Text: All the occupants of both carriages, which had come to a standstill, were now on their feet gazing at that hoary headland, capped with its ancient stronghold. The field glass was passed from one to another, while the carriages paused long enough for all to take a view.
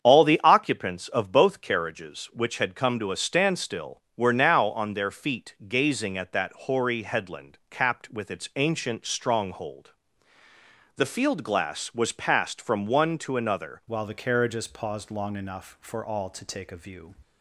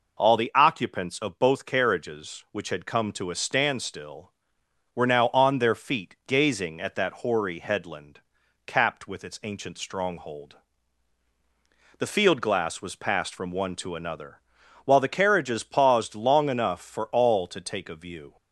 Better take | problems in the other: second | starts louder than the rest; strong; until 1.0 s; 8 dB // changes voice at "while"; from 13.8 s on; 3.3 s long

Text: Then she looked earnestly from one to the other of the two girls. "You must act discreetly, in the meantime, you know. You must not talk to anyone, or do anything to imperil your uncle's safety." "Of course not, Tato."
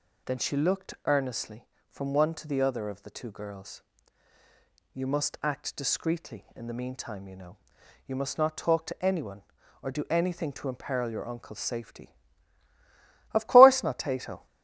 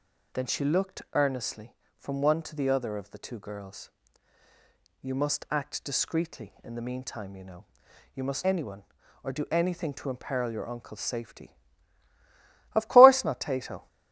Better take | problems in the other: first | skips "not talk to"; at 8.4 s

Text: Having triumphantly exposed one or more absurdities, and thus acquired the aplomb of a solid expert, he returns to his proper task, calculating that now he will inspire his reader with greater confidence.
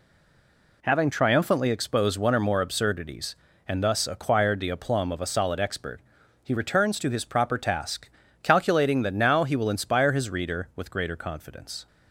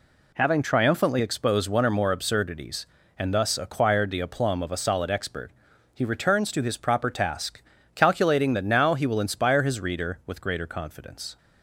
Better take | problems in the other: second | stays silent before the first word; slight; until 0.8 s; 0.8 s long

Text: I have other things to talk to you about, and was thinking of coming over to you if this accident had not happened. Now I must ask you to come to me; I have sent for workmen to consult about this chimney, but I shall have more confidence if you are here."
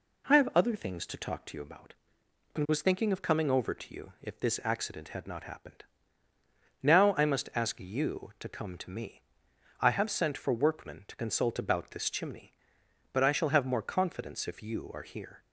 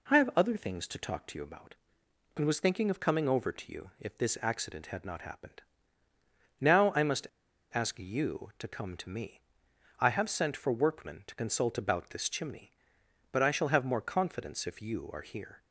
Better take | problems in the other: first | pauses between "must" and "ask"; noticeable; at 7.2 s; 0.47 s long

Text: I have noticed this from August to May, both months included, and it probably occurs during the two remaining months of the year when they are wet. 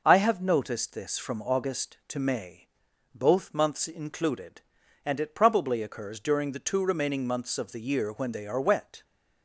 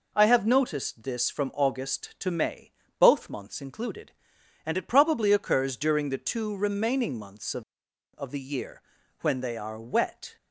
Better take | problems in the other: first | says "of" twice; at 8.1 s // pauses between "year" and "when"; at 8.8 s; 0.42 s long

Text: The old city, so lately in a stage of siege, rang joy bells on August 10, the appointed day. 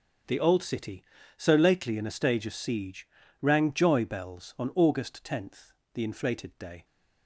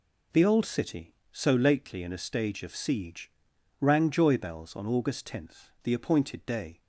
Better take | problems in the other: second | starts louder than the rest; until 1.6 s; 6.5 dB // says "inflated" for "appointed"; at 6.0 s

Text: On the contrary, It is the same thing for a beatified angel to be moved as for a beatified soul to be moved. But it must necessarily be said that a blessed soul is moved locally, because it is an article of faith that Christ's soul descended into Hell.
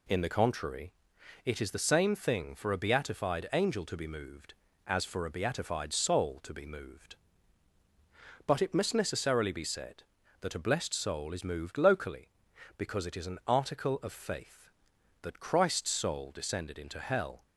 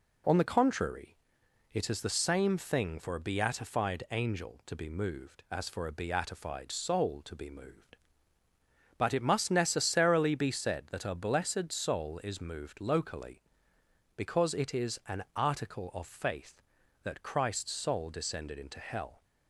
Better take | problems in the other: second | says "In" for "On"; at 0.0 s

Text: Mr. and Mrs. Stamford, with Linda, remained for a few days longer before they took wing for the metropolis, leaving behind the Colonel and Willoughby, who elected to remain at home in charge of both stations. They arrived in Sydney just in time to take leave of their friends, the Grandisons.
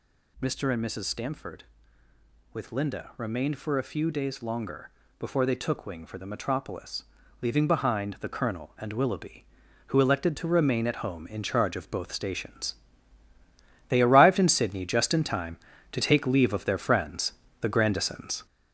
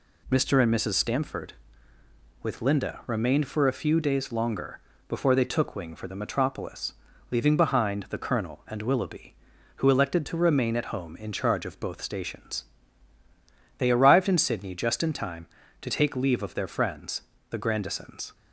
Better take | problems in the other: second | gets louder; noticeable; throughout; 6 dB // pauses between "longer" and "before"; slight; at 4.8 s; 0.28 s long; slight in the second

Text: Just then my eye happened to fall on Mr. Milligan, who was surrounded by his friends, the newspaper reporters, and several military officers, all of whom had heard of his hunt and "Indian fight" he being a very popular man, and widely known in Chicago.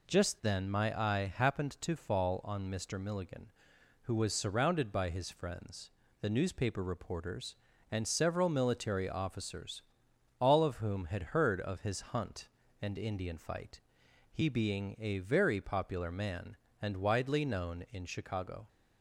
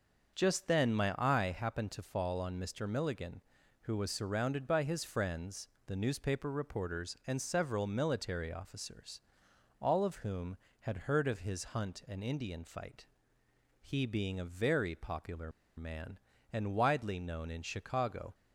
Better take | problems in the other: first | starts louder than the rest; until 1.3 s; 6.5 dB // pauses between "fight" and "he"; noticeable; at 13.0 s; 0.74 s long; noticeable in the first // pauses between "popular" and "man"; slight; at 15.5 s; 0.26 s long

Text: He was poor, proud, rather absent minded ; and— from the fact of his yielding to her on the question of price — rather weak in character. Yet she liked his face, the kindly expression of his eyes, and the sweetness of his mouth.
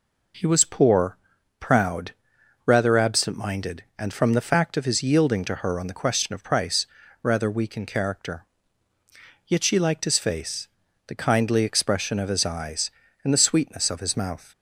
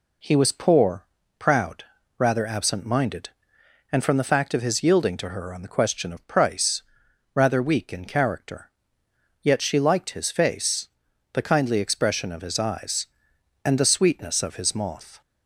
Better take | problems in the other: first | says "moth" for "mouth"; at 14.7 s

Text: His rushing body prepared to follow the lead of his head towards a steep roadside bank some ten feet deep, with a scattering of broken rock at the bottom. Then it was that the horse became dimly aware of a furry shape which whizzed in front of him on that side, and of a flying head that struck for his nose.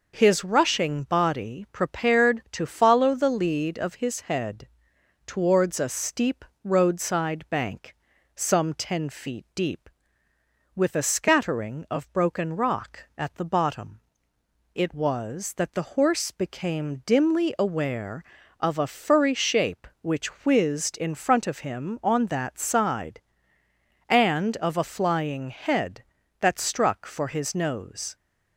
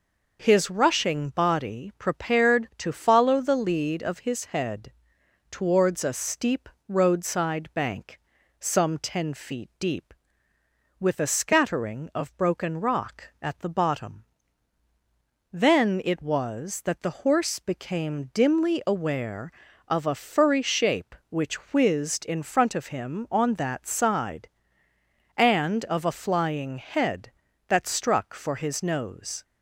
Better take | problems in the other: second | pauses between "head" and "towards"; noticeable; at 4.6 s; 0.58 s long; noticeable in the second // pauses between "steep" and "roadside"; slight; at 6.4 s; 0.18 s long; slight in the second // pauses between "bank" and "some"; at 7.9 s; 0.40 s long; also in the second // skips "Then"; at 14.3 s

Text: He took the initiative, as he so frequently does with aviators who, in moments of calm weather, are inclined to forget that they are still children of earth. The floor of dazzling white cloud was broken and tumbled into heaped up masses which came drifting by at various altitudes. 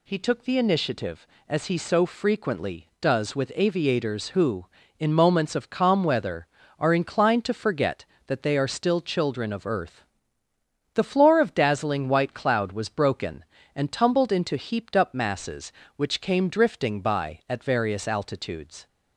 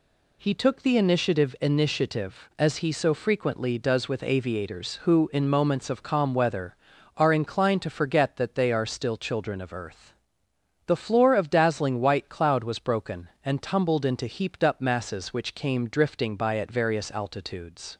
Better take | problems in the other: first | says "initiative" twice; at 1.5 s

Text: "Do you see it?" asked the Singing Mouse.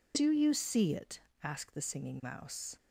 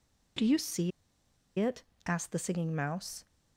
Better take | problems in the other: first | pauses between "see" and "it"; noticeable; at 0.9 s; 0.68 s long

